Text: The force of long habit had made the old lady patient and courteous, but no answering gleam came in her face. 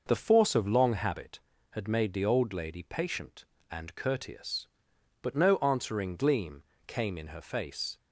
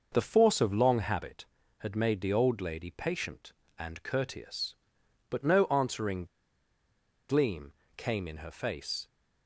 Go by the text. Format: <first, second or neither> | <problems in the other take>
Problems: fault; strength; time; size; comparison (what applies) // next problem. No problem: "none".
first | pauses between "answering" and "gleam"; at 6.2 s; 1.0 s long // pauses between "gleam" and "came"; slight; at 7.7 s; 0.24 s long; slight in the first